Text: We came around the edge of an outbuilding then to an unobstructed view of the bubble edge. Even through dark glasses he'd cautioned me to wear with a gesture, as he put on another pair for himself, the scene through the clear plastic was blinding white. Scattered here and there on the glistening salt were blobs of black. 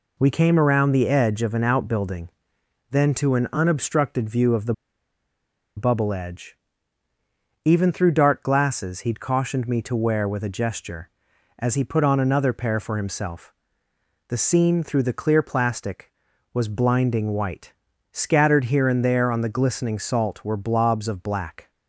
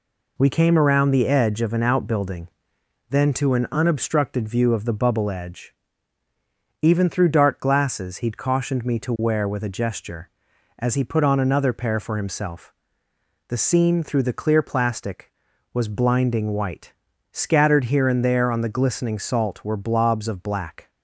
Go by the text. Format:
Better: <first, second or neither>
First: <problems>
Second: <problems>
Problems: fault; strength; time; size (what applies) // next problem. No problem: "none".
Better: second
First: pauses between "outbuilding" and "then"; noticeable; at 2.2 s; 0.62 s long // pauses between "the" and "bubble"; at 4.7 s; 1.0 s long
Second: pauses between "outbuilding" and "then"; noticeable; at 2.4 s; 0.62 s long